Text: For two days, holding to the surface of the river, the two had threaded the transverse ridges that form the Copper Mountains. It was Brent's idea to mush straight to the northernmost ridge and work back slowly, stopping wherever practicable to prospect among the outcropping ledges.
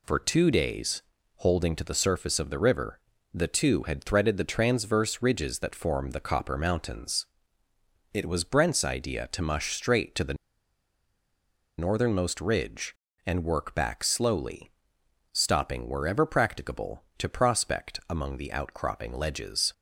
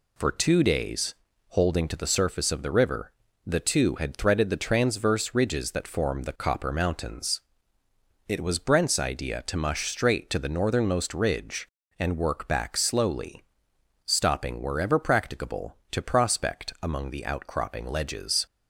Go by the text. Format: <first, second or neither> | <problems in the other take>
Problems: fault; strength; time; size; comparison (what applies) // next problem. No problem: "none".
second | pauses between "the" and "northernmost"; strong; at 10.3 s; 1.4 s long